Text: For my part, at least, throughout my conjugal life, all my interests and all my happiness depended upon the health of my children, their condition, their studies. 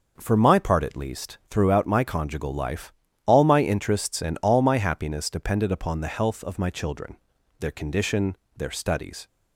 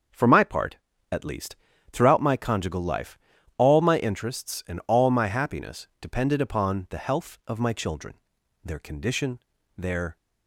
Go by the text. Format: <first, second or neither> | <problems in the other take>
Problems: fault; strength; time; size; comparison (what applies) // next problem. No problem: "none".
first | starts louder than the rest; until 1.4 s; 6.5 dB // stops before "studies"; at 10.1 s